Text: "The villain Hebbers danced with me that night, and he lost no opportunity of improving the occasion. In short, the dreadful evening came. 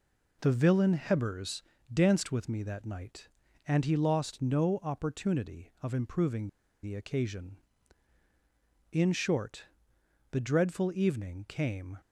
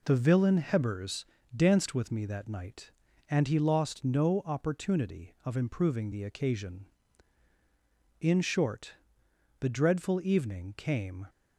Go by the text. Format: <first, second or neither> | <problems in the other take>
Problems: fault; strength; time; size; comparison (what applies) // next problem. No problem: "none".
second | pauses between "Hebbers" and "danced"; slight; at 1.6 s; 0.30 s long; slight in the second // pauses between "improving" and "the"; slight; at 6.4 s; 0.35 s long